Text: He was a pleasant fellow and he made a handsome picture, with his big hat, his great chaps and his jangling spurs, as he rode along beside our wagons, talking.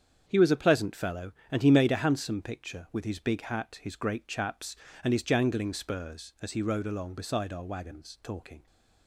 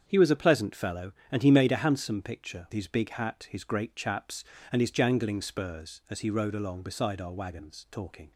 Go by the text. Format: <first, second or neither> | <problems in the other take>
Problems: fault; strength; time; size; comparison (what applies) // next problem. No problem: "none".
first | starts louder than the rest; strong; until 1.0 s; 7.5 dB; strong in the first // skips "with"; at 2.6 s